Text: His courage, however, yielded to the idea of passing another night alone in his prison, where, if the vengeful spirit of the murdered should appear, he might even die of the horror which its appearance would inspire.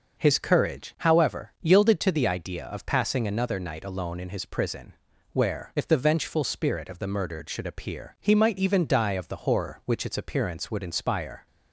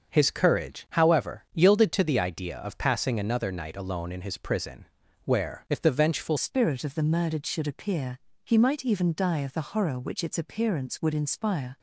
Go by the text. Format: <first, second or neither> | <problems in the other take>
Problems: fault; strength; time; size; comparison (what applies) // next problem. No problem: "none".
first | starts louder than the rest; until 1.1 s; 6 dB // changes voice at "spirit"; from 6.3 s on; 5.4 s long